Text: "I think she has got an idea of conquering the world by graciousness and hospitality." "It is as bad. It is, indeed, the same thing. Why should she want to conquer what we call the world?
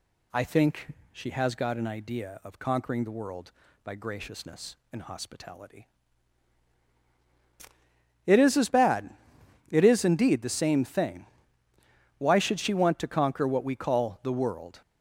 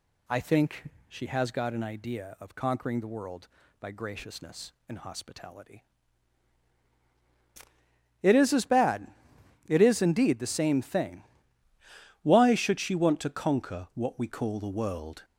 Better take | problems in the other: first | pauses between "think" and "she"; slight; at 0.9 s; 0.18 s long; slight in the first // changes voice at "Why"; from 12.2 s on; 3.0 s long

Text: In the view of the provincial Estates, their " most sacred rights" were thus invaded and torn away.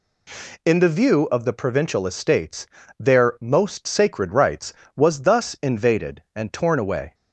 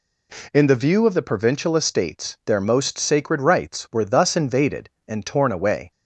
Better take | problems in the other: second | says "was" for "were"; at 4.9 s

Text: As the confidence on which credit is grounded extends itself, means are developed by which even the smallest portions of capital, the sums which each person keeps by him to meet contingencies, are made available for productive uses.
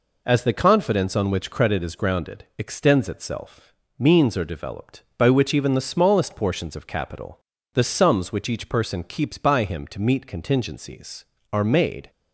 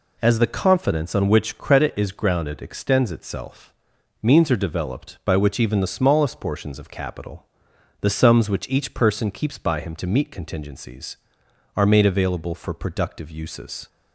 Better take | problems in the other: second | stops before "available for productive uses"; at 12.0 s

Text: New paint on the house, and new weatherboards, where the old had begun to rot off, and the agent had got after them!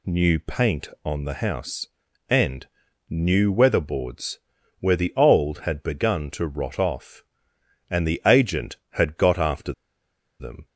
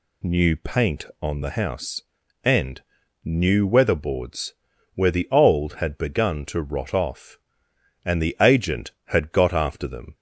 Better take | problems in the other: second | pauses between "and" and "new"; at 2.6 s; 0.42 s long; also in the second // pauses between "after" and "them"; noticeable; at 9.7 s; 0.66 s long

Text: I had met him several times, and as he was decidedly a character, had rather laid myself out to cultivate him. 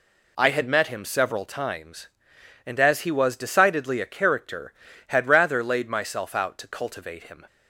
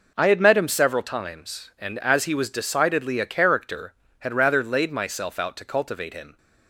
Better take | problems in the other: neither | none

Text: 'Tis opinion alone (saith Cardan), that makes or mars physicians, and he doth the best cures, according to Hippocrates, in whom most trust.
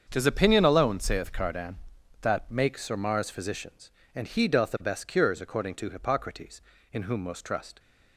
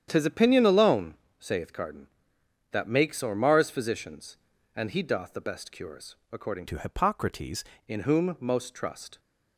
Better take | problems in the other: first | starts louder than the rest; strong; until 1.1 s; 9.5 dB; strong in the first // changes voice from "to" to "Hippocrates"; from 6.6 to 7.6 s; 1.0 s long

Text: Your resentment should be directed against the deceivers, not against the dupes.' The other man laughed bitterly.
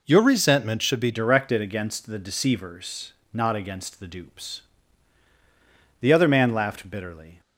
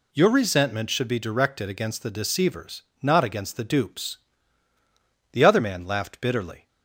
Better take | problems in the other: second | changes voice at "directed"; from 1.1 s on; 6.2 s long

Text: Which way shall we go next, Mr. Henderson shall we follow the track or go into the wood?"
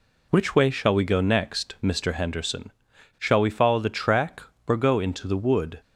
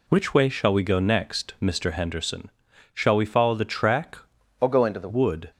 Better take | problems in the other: first | pauses between "Henderson" and "shall"; at 2.4 s; 0.44 s long; noticeable in the first // changes voice from "or" to "the"; from 4.6 to 5.0 s; 0.4 s long

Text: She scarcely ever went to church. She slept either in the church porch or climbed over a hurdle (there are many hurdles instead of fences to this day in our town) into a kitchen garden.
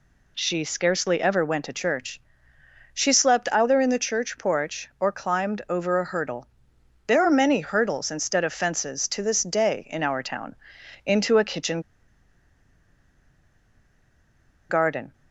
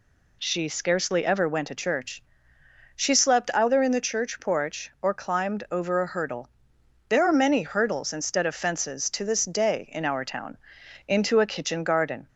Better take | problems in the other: second | pauses between "kitchen" and "garden"; strong; at 11.7 s; 2.8 s long

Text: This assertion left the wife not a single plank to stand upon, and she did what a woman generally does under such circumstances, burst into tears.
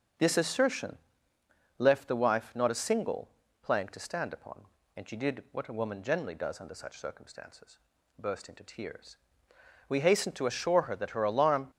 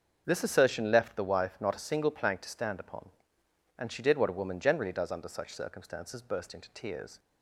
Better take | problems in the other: second | starts louder than the rest; until 1.9 s; 6.5 dB; also in the second // pauses between "assertion" and "left"; noticeable; at 0.9 s; 0.80 s long // pauses between "single" and "plank"; slight; at 3.2 s; 0.34 s long // goes on to say "We hastened to assure her that her alarm"; strong; from 9.8 s on; 1.8 s long

